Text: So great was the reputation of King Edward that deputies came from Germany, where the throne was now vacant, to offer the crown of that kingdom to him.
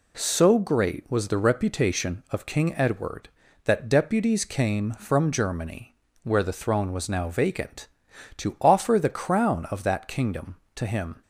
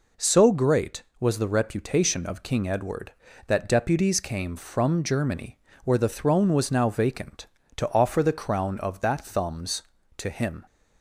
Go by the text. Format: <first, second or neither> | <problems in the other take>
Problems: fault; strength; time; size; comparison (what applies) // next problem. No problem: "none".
first | says "thumbs" for "kingdom"; at 9.2 s